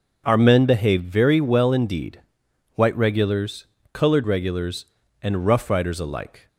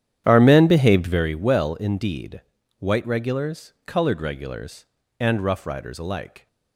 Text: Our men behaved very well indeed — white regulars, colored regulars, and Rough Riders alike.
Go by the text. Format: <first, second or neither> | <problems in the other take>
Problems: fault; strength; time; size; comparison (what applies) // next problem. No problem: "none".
first | starts louder than the rest; strong; until 1.3 s; 10 dB